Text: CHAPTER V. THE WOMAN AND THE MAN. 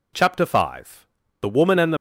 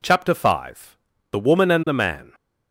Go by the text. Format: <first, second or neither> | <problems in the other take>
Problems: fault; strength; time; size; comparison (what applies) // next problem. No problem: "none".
second | stops before "MAN"; at 1.9 s